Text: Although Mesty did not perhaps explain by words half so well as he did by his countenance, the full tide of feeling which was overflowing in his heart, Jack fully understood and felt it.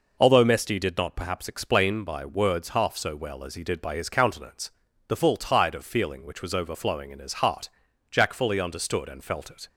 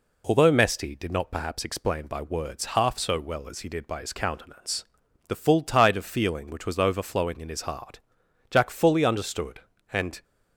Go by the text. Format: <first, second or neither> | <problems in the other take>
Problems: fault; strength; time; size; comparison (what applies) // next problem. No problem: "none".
first | stops before "felt it"; at 10.2 s